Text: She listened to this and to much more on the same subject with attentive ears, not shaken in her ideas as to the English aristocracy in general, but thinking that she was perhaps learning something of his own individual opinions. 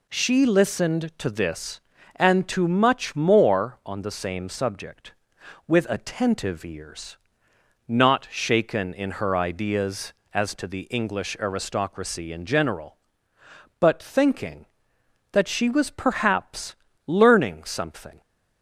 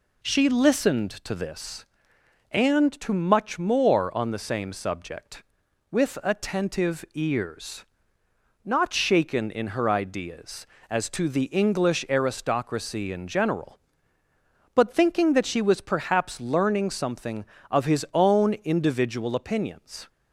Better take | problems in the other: second | pauses between "perhaps" and "learning"; slight; at 16.7 s; 0.32 s long // stops before "of his own individual opinions"; at 18.2 s

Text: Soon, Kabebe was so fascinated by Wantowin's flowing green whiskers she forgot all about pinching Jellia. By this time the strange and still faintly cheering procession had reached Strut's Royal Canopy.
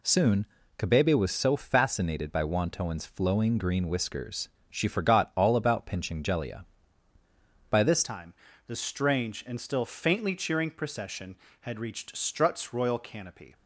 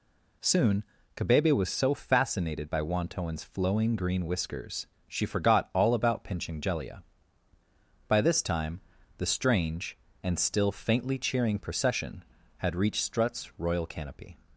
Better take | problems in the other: second | pauses between "whiskers" and "she"; slight; at 4.4 s; 0.20 s long; slight in the second // changes voice at "time"; from 8.0 s on; 5.5 s long // pauses between "time" and "the"; slight; at 8.3 s; 0.34 s long; also in the second

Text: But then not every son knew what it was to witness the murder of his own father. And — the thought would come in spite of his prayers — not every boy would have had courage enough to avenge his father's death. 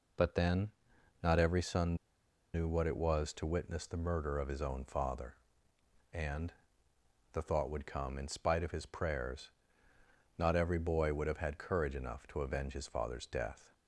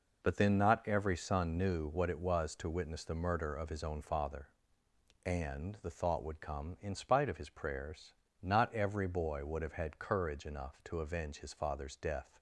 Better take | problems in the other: second | pauses between "then" and "not"; noticeable; at 0.7 s; 0.52 s long // pauses between "son" and "knew"; noticeable; at 1.9 s; 0.59 s long

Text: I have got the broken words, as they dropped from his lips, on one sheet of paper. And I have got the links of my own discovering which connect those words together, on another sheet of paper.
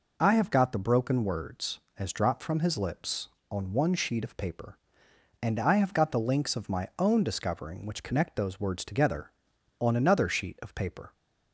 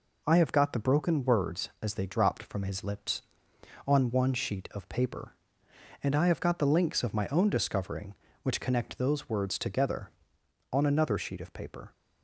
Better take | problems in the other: second | skips "they"; at 2.1 s

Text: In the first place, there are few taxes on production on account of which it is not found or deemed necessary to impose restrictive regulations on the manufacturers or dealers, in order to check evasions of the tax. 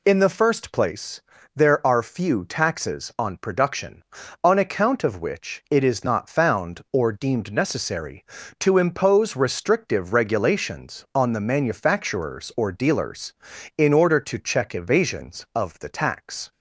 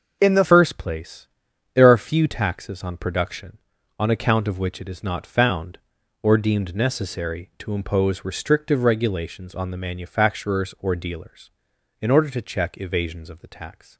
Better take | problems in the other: first | starts louder than the rest; until 1.2 s; 6 dB // changes voice at "first"; from 0.4 s on; 13.5 s long

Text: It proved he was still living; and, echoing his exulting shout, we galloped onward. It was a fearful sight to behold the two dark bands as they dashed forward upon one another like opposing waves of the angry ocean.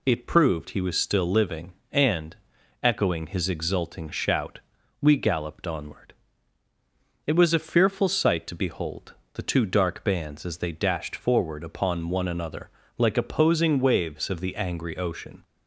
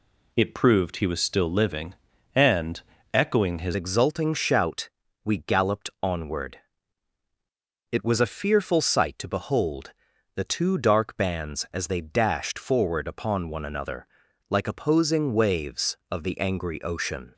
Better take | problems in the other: first | changes voice at "exulting"; from 3.7 s on; 13.6 s long // pauses between "behold" and "the"; at 9.9 s; 0.42 s long; slight in the first // pauses between "another" and "like"; at 14.0 s; 0.42 s long; slight in the first

